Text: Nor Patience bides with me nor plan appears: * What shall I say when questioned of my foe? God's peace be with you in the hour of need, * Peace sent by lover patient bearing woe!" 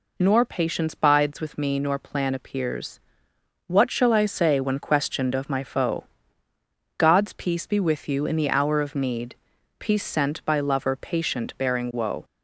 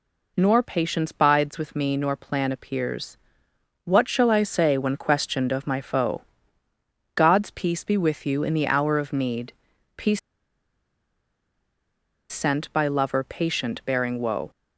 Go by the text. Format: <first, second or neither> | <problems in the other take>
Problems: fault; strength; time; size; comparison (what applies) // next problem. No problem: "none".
first | pauses between "Peace" and "sent"; strong; at 10.1 s; 2.1 s long